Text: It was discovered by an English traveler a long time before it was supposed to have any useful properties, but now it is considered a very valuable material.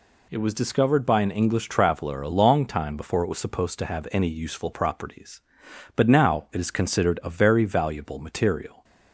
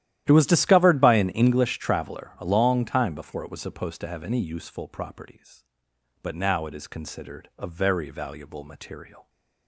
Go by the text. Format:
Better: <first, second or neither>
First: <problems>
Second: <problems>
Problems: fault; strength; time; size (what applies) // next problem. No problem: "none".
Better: first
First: none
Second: starts louder than the rest; strong; until 1.6 s; 12.5 dB